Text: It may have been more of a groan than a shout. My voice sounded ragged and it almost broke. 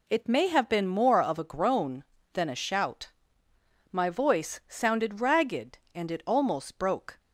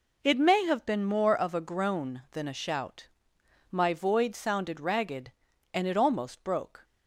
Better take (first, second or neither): first